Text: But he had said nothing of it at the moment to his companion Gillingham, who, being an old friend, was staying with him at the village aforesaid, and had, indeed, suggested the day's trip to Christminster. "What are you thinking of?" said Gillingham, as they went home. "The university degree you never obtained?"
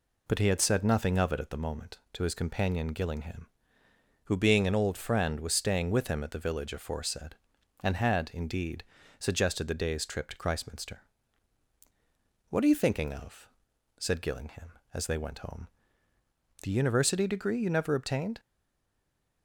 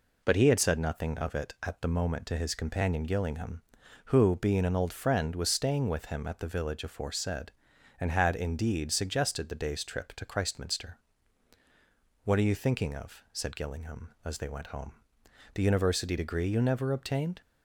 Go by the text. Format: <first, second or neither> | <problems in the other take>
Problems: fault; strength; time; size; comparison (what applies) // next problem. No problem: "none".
second | stays silent after the last word; from 18.3 s on; 1.1 s long